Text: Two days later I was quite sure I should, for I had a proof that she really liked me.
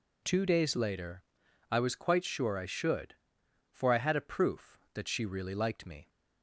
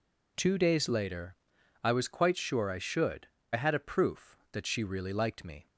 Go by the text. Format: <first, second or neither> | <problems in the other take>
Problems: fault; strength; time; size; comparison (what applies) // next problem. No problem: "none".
first | pauses between "later" and "I"; noticeable; at 1.3 s; 0.48 s long; noticeable in the first // skips "for"; at 3.3 s